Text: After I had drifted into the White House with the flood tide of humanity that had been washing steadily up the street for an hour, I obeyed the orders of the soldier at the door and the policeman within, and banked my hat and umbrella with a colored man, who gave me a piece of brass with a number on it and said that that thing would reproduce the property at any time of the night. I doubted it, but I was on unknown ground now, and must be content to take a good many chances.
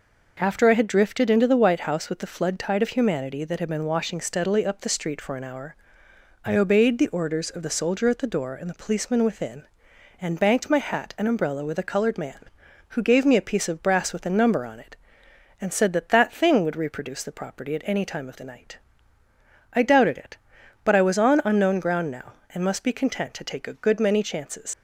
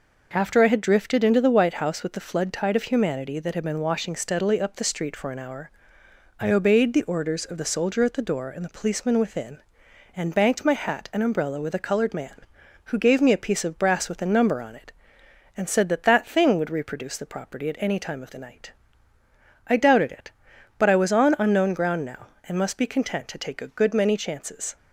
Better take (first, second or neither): second